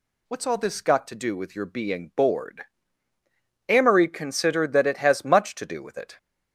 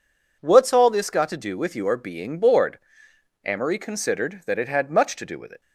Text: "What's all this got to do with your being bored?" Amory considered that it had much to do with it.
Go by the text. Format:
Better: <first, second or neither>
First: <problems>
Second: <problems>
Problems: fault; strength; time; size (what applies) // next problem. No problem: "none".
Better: second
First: says "has" for "had"; at 4.9 s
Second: none